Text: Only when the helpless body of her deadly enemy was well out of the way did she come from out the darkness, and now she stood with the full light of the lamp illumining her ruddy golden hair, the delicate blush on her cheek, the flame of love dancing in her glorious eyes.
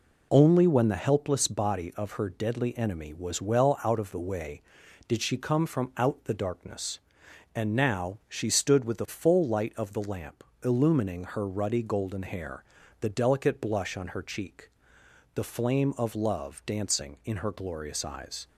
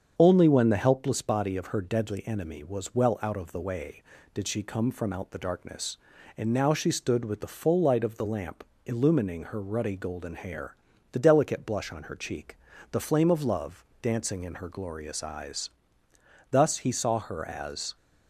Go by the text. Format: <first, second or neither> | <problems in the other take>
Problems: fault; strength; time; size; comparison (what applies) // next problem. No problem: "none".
first | starts louder than the rest; strong; until 1.1 s; 7 dB // pauses between "lamp" and "illumining"; slight; at 8.6 s; 0.22 s long; slight in the first // pauses between "love" and "dancing"; slight; at 13.8 s; 0.20 s long // goes on to say "Thus he saw her as"; from 16.5 s on; 1.4 s long